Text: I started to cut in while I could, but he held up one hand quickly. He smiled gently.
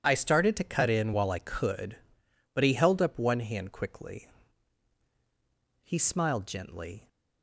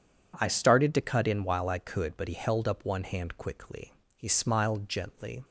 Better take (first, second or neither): neither